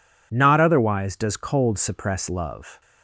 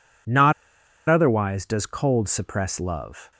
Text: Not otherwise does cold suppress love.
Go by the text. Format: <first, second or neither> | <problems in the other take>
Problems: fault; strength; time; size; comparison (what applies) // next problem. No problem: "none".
first | pauses between "Not" and "otherwise"; noticeable; at 0.5 s; 0.56 s long